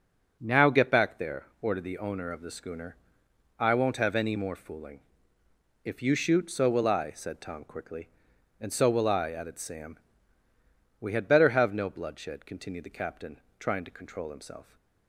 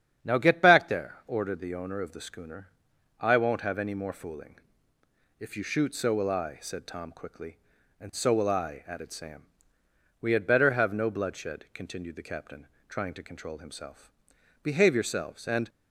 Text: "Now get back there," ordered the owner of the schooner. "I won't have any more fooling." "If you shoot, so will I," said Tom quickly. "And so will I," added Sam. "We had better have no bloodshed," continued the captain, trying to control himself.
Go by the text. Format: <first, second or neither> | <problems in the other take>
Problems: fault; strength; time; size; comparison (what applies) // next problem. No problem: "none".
first | starts louder than the rest; strong; until 1.3 s; 8.5 dB // goes on to say "Behave yourselves and"; noticeable; from 14.6 s on; 1.0 s long